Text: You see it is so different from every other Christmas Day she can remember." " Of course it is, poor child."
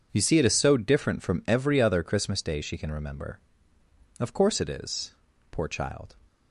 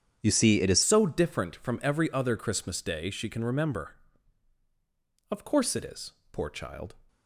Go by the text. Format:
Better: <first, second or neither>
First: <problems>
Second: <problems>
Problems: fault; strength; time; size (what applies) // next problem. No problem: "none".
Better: first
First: starts louder than the rest; strong; until 1.1 s; 8 dB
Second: starts louder than the rest; strong; until 1.2 s; 9.5 dB // changes voice at "so"; from 0.8 s on; 6.1 s long